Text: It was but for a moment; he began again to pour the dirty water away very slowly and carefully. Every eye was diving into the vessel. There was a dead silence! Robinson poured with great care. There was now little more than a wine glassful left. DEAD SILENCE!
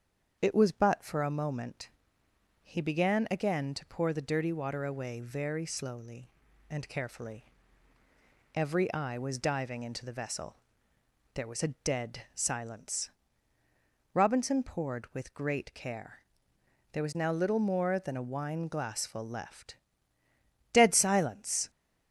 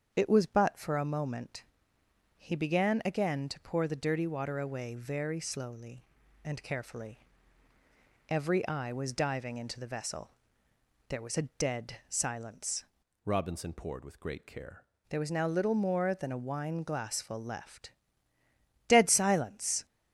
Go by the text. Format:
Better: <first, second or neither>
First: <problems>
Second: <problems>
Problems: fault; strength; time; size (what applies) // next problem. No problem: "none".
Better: first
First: starts louder than the rest; strong; until 1.4 s; 7.5 dB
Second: starts louder than the rest; strong; until 1.1 s; 7.5 dB // changes voice from "Robinson" to "care"; from 13.2 to 14.8 s; 1.6 s long